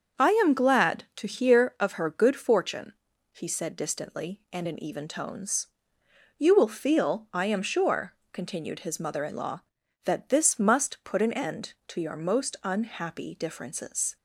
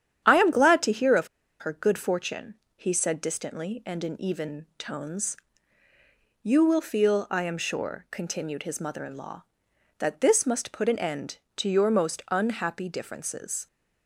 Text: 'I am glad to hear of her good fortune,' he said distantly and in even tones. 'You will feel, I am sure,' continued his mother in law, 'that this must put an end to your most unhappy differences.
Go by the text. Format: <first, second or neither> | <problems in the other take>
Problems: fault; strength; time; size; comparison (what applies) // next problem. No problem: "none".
first | starts louder than the rest; strong; until 1.2 s; 9.5 dB; also in the first // pauses between "of" and "her"; slight; at 1.2 s; 0.33 s long